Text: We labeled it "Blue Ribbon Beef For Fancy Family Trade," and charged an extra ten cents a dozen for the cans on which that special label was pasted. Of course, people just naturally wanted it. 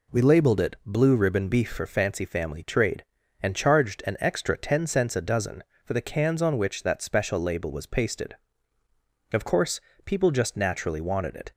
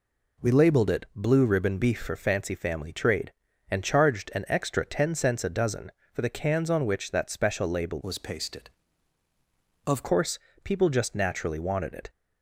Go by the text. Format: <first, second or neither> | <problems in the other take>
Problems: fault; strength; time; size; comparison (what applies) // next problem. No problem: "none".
first | changes voice from "was" to "Of"; from 8.0 to 10.0 s; 2.0 s long